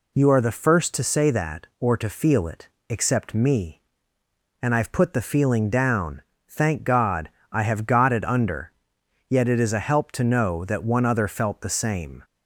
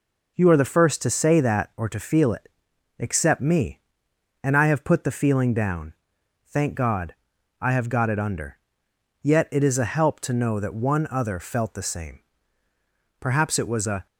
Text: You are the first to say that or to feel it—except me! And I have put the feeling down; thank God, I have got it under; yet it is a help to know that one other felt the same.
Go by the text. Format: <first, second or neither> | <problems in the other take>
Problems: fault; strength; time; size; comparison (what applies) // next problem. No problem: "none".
first | goes on to say "Perhaps it was a"; noticeable; from 13.1 s on; 0.86 s long